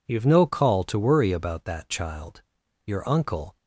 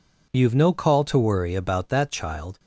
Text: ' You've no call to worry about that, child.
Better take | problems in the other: second | goes on to say "Your uncle"; noticeable; from 2.8 s on; 0.72 s long

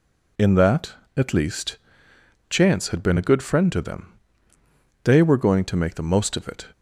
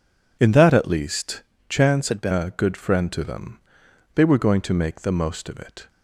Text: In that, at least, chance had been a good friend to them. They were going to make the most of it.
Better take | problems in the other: first | changes voice from "had" to "been"; from 2.0 to 2.3 s; 0.3 s long

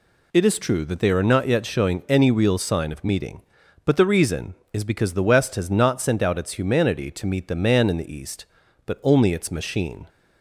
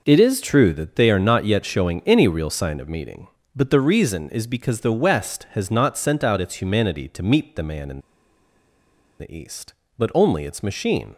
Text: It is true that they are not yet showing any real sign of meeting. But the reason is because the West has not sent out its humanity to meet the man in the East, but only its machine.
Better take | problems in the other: first | pauses between "in" and "the"; at 8.0 s; 1.1 s long

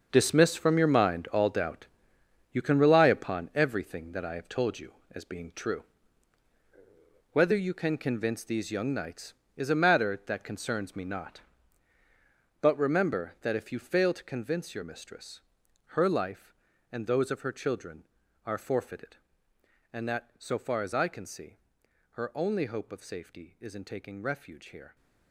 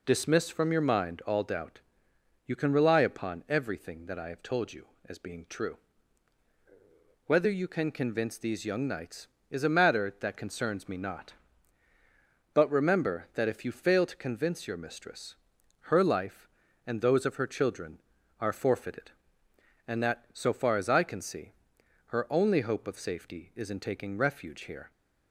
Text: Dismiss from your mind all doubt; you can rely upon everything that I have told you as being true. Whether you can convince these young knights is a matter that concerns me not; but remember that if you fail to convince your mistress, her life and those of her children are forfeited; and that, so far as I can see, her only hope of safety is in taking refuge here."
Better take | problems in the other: second | gets quieter; strong; throughout; 12.5 dB

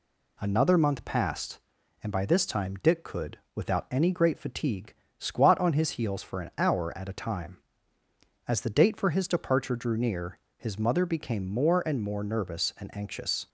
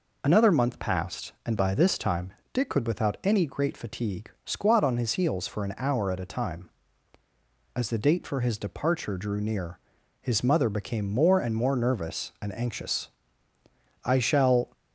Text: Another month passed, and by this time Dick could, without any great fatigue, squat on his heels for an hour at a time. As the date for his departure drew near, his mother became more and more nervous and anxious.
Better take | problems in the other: first | pauses between "time" and "Dick"; slight; at 2.3 s; 0.20 s long // goes on to say "I shall"; noticeable; from 14.0 s on; 0.70 s long

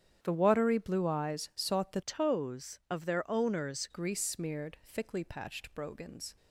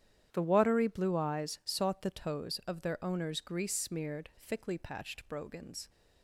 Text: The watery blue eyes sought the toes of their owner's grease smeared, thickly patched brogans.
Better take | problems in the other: second | starts louder than the rest; strong; until 1.2 s; 9.5 dB; strong in the second // changes voice from "toes" to "owner's"; from 2.0 to 3.8 s; 1.8 s long

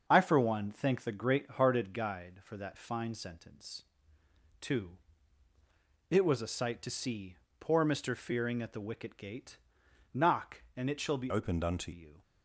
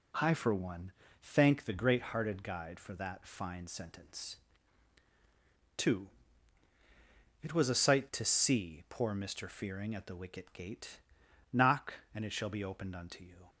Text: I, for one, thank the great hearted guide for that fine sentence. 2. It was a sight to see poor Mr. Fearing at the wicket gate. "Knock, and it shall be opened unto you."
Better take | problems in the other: second | starts louder than the rest; until 1.0 s; 6.5 dB // pauses between "see" and "poor"; slight; at 7.3 s; 0.24 s long // changes voice from "opened" to "unto"; from 11.2 to 11.9 s; 0.7 s long

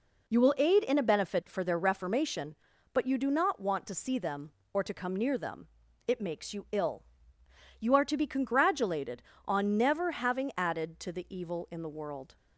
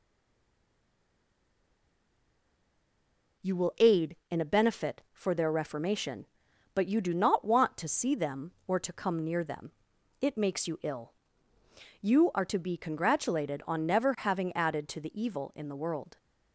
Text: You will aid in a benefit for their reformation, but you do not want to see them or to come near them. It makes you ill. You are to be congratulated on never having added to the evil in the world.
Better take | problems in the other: first | stays silent before the first word; strong; until 3.4 s; 3.4 s long

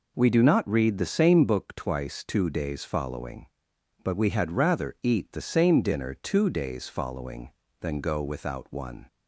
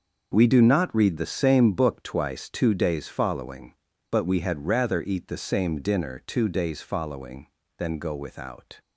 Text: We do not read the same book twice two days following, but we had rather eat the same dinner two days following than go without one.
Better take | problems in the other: first | starts louder than the rest; noticeable; until 1.3 s; 6 dB // stops before "one"; at 8.7 s

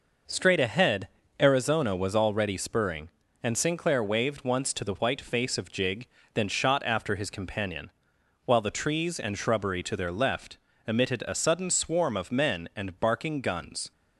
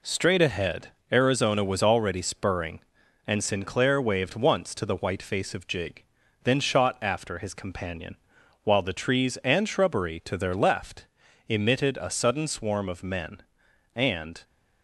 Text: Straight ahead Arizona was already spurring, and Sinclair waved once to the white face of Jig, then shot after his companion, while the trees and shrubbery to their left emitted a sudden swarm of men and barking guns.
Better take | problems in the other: first | pauses between "ahead" and "Arizona"; slight; at 0.8 s; 0.24 s long; slight in the first // pauses between "left" and "emitted"; at 11.0 s; 0.42 s long; slight in the first // stops before "barking guns"; at 14.4 s

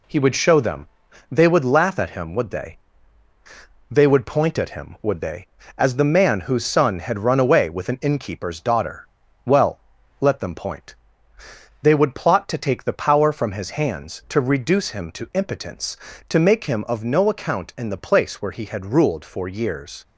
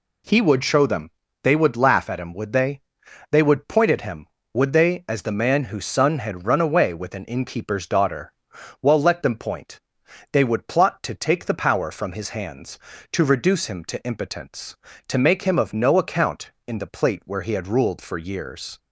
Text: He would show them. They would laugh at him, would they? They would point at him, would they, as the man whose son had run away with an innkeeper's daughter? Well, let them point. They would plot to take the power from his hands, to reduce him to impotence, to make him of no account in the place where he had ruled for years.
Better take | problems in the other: first | says "plate" for "place"; at 16.8 s

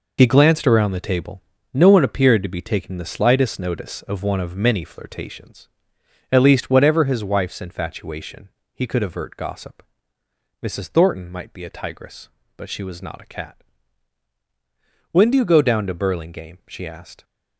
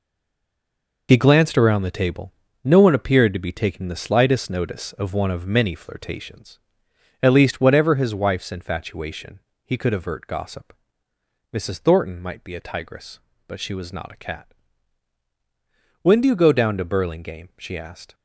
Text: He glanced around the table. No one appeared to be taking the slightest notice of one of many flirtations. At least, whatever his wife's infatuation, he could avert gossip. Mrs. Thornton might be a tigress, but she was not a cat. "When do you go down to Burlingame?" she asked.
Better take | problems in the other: first | stays silent before the first word; until 1.0 s; 1.0 s long

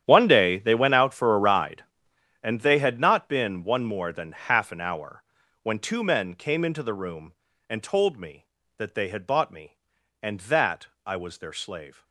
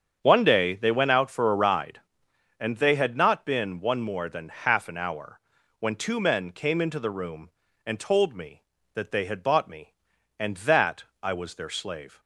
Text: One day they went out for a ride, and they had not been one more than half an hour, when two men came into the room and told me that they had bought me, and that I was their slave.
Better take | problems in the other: second | gets quieter; strong; throughout; 16.5 dB // starts louder than the rest; strong; until 1.0 s; 10 dB; strong in the second // pauses between "that" and "I"; slight; at 10.8 s; 0.18 s long; slight in the second

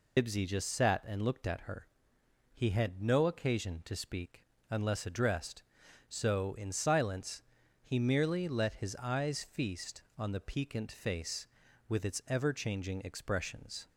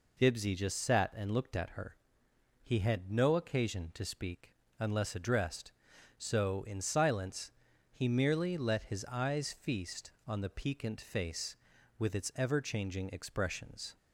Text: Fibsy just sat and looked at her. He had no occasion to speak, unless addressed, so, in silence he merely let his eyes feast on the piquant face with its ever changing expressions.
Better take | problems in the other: second | loses the start of "Fibsy"; at 0.1 s; 80 ms // pauses between "silence" and "he"; at 7.4 s; 0.40 s long; also in the second

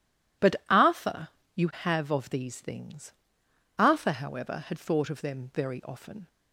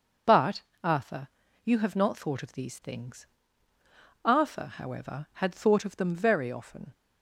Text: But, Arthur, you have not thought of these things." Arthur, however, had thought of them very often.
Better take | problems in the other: second | skips "not thought"; at 2.0 s

